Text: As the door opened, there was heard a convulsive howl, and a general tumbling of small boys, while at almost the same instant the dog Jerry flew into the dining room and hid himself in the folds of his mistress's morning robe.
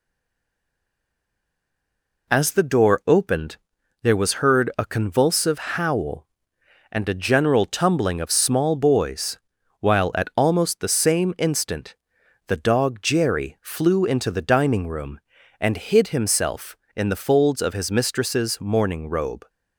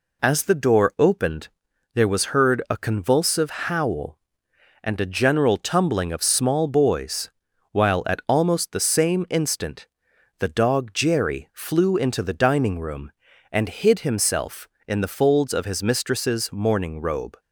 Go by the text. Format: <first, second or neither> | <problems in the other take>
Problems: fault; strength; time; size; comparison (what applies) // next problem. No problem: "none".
second | stays silent before the first word; until 2.2 s; 2.2 s long // pauses between "instant" and "the"; noticeable; at 11.9 s; 0.52 s long; noticeable in the second